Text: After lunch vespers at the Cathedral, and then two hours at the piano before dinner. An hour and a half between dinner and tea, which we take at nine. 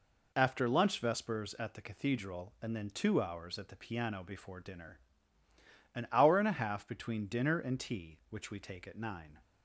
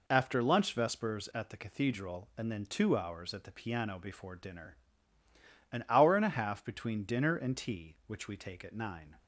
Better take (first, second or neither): neither